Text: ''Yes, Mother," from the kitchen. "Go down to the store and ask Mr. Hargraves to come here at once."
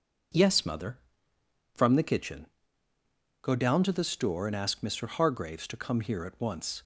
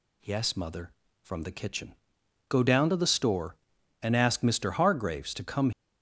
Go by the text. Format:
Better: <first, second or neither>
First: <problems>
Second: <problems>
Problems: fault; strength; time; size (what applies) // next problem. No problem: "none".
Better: first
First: none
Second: stops before "here at once"; at 5.7 s